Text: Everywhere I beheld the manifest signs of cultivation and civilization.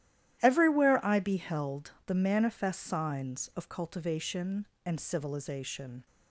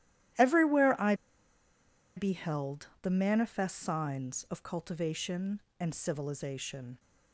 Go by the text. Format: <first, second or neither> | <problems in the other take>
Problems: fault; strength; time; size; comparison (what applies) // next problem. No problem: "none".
first | starts louder than the rest; strong; until 2.3 s; 13 dB; strong in the first // pauses between "I" and "beheld"; at 1.1 s; 1.0 s long